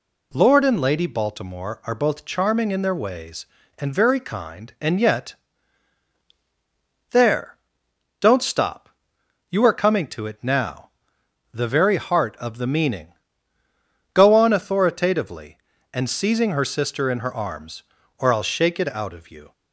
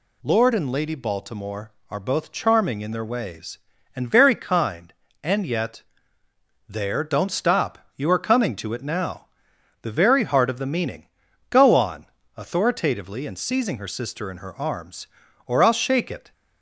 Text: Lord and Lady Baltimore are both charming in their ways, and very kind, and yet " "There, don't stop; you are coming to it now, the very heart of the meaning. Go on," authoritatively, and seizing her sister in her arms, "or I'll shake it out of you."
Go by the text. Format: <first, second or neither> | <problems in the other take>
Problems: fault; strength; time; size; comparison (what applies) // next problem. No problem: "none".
first | stops before "out of you"; at 16.3 s